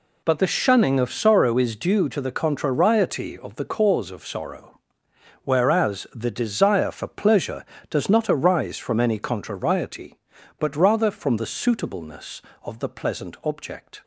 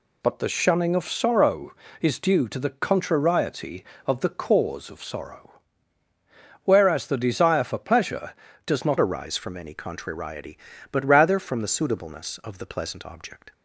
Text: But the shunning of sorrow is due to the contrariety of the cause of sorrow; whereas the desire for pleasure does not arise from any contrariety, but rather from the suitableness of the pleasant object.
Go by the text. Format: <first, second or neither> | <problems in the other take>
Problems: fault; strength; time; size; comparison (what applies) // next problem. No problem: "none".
first | changes voice at "arise"; from 8.9 s on; 4.6 s long